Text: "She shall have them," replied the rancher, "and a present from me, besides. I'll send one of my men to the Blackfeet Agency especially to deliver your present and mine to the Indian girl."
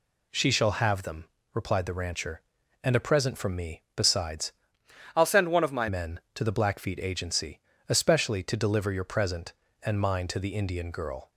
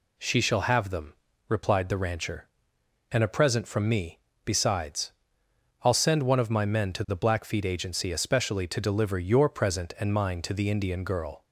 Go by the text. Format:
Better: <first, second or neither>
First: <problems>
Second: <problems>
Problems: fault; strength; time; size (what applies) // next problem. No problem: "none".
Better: second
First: changes voice from "I'll" to "my"; from 5.1 to 5.8 s; 0.7 s long // pauses between "Agency" and "especially"; slight; at 7.6 s; 0.28 s long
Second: none